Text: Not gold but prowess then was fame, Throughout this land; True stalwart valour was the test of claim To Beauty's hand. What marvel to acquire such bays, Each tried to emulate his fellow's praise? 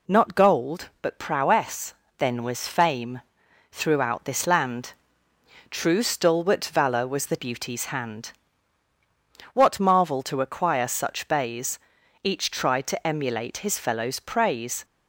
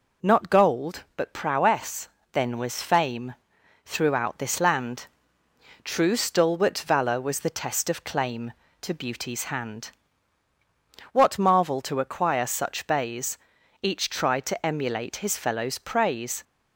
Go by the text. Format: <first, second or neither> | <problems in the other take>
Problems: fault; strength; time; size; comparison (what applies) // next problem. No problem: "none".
second | pauses between "prowess" and "then"; slight; at 1.9 s; 0.24 s long; slight in the second // skips "test of claim To"; at 7.3 s